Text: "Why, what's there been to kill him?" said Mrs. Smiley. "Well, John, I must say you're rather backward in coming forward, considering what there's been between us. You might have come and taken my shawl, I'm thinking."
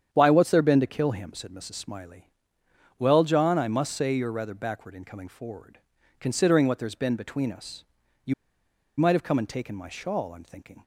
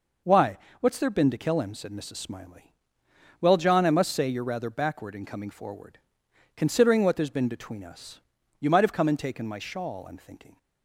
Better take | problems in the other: second | starts louder than the rest; strong; until 1.1 s; 8.5 dB // pauses between "You" and "might"; noticeable; at 8.3 s; 0.65 s long

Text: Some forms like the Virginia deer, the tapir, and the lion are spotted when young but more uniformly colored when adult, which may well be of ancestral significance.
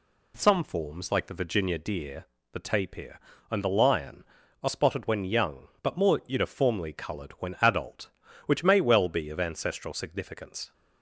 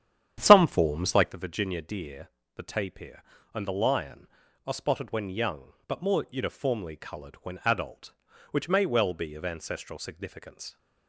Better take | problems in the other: first | starts louder than the rest; strong; until 1.4 s; 10 dB

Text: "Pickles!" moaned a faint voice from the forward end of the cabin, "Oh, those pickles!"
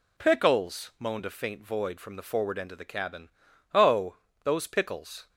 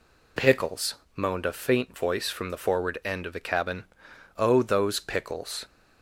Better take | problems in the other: second | says "void" for "voice"; at 1.6 s

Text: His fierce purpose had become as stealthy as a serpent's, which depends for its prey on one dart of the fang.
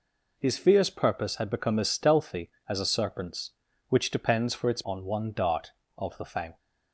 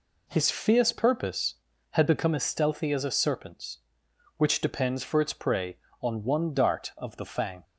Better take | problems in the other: second | skips "prey"; at 4.8 s

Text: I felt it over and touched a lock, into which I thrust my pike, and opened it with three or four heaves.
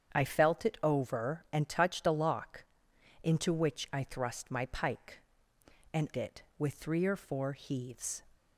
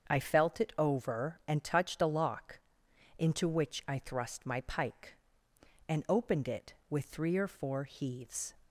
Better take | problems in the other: second | starts louder than the rest; strong; until 1.2 s; 8 dB; also in the second // skips "opened"; at 6.1 s

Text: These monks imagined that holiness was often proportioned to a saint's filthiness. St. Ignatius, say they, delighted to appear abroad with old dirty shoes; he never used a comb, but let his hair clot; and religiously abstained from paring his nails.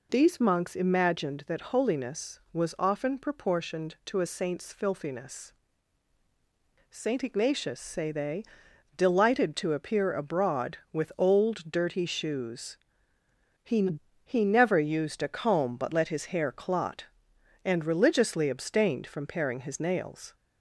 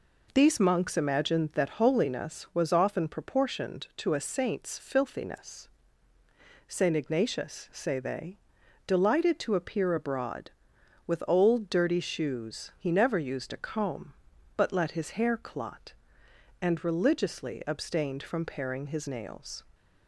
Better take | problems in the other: second | says "he" twice; at 14.2 s

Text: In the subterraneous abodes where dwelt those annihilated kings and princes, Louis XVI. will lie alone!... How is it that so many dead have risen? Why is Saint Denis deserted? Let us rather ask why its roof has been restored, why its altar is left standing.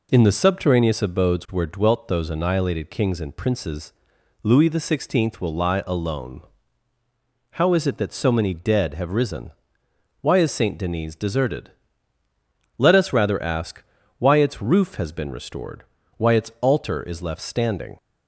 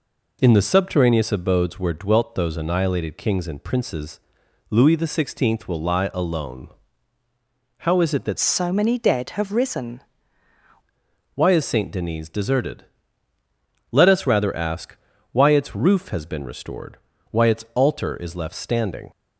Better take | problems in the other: first | changes voice from "so" to "risen"; from 8.3 to 10.0 s; 1.7 s long // pauses between "ask" and "why"; slight; at 14.9 s; 0.36 s long; slight in the first

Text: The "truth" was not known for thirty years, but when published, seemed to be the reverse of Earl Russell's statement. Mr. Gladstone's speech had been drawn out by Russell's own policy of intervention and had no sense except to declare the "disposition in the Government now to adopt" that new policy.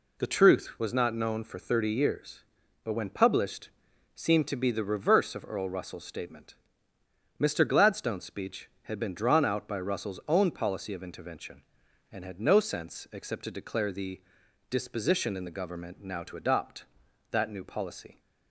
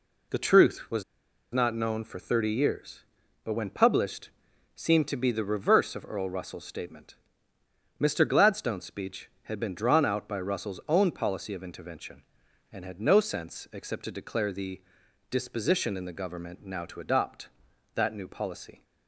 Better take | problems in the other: first | pauses between "was" and "not"; noticeable; at 1.0 s; 0.51 s long // pauses between "the" and "disposition"; noticeable; at 14.7 s; 0.52 s long; noticeable in the first

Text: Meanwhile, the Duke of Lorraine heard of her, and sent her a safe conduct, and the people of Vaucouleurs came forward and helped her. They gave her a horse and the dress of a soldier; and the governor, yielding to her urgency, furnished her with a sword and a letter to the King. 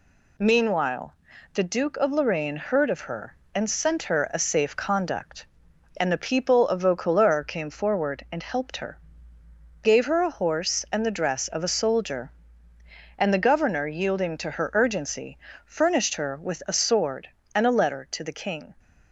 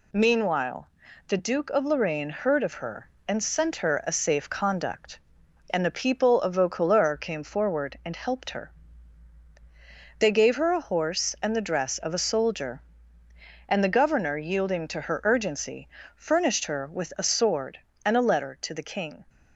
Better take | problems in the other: second | skips "They"; at 9.4 s

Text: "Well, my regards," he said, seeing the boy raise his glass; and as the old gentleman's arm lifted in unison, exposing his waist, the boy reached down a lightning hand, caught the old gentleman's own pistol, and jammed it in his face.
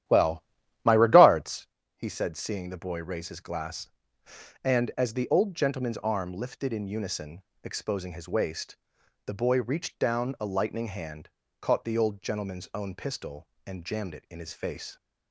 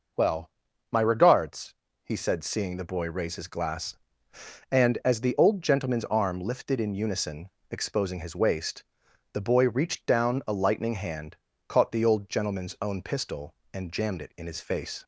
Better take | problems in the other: second | starts louder than the rest; strong; until 1.8 s; 11.5 dB

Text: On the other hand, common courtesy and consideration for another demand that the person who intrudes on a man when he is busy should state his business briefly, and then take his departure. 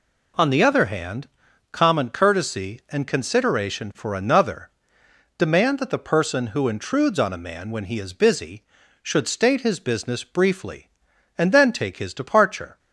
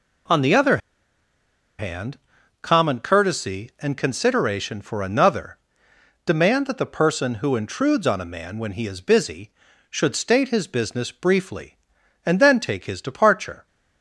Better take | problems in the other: first | pauses between "other" and "hand"; at 0.7 s; 1.0 s long // pauses between "another" and "demand"; noticeable; at 5.5 s; 0.70 s long; noticeable in the first

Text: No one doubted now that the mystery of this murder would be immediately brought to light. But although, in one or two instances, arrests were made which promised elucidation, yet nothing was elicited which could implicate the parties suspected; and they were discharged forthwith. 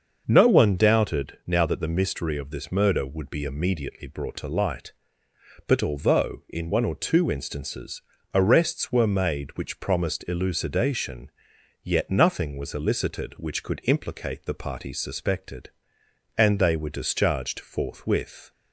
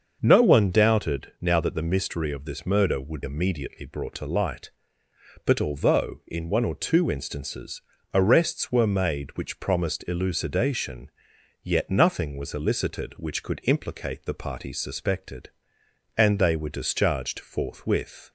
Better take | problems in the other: first | starts louder than the rest; until 1.2 s; 6.5 dB; also in the first // skips "be"; at 3.2 s

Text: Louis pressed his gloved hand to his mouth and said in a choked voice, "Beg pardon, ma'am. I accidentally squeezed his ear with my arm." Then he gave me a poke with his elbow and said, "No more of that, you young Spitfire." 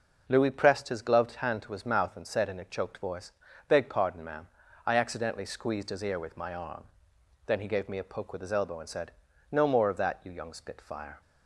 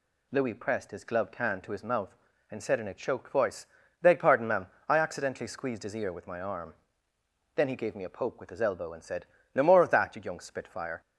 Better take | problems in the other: neither | none

